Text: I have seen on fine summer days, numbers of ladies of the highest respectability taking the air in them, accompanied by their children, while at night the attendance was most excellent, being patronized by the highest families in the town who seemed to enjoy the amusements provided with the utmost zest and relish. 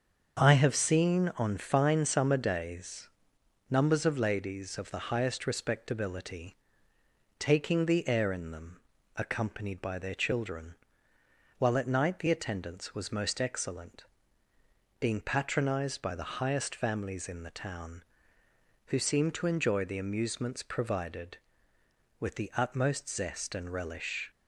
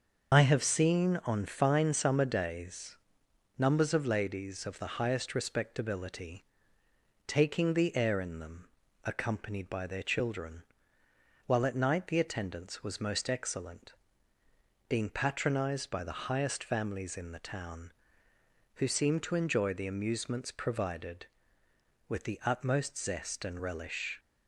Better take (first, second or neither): first